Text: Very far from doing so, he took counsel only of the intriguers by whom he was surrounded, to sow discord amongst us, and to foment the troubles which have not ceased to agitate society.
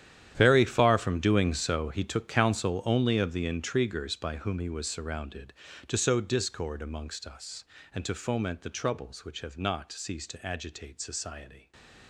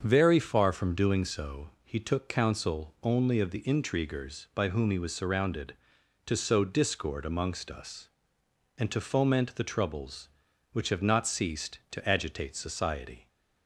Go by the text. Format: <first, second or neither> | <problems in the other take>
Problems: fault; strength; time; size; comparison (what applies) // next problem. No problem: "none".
second | gets quieter; strong; throughout; 15.5 dB // starts louder than the rest; strong; until 1.3 s; 10.5 dB; also in the second // stays silent after the last word; slight; from 11.4 s on; 0.6 s long